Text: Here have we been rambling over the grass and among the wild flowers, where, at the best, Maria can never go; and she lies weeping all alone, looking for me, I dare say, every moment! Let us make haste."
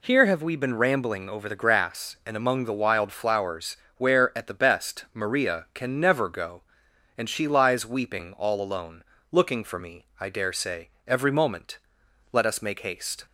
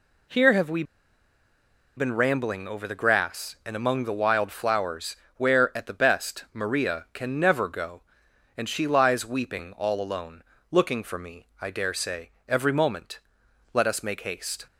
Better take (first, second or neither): first